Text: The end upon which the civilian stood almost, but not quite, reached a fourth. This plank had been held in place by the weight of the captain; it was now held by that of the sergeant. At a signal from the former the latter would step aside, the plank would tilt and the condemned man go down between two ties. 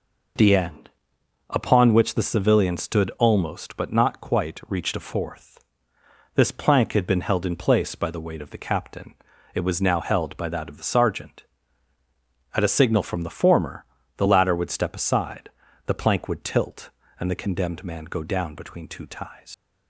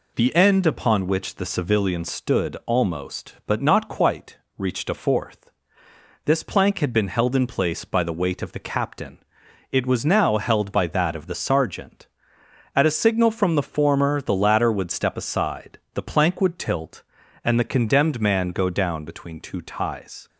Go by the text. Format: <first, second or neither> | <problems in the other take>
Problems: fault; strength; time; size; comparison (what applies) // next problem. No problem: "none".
second | pauses between "end" and "upon"; noticeable; at 0.9 s; 0.58 s long // pauses between "former" and "the"; slight; at 13.8 s; 0.30 s long // leaves "ties" unfinished; at 19.5 s; 80 ms